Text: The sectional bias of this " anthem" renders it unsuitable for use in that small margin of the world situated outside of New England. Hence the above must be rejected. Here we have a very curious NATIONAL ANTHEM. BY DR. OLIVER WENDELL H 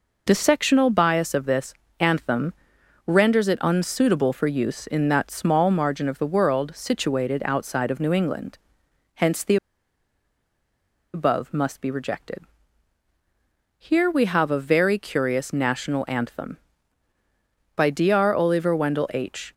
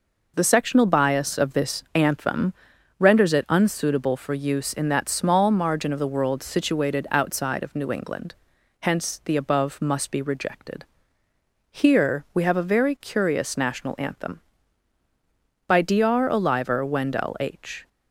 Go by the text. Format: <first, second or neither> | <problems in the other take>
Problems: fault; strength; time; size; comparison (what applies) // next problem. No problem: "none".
second | pauses between "anthem" and "renders"; noticeable; at 2.5 s; 0.54 s long; noticeable in the second // pauses between "the" and "above"; strong; at 9.5 s; 1.5 s long